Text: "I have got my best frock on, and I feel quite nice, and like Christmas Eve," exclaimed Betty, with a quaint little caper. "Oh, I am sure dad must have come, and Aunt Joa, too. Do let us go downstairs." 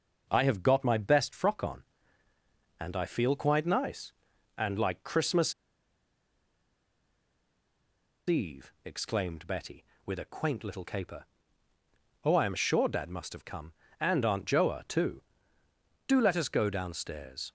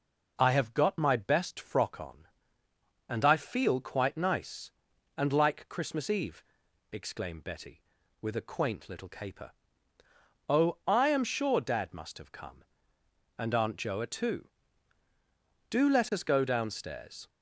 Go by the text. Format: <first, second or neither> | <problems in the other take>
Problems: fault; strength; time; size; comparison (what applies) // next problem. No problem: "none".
second | starts louder than the rest; until 1.3 s; 6.5 dB // pauses between "Christmas" and "Eve"; strong; at 5.5 s; 2.7 s long